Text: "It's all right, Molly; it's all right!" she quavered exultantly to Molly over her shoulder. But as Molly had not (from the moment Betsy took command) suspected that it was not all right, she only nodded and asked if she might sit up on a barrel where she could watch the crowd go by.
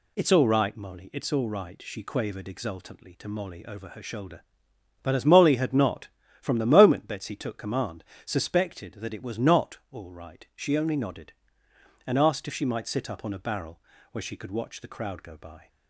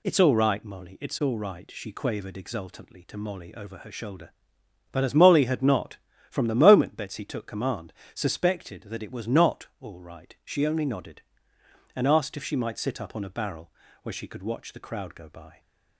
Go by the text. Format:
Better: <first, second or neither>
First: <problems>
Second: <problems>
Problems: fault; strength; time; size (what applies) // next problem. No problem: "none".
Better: neither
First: pauses between "barrel" and "where"; slight; at 13.8 s; 0.32 s long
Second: pauses between "barrel" and "where"; slight; at 13.7 s; 0.32 s long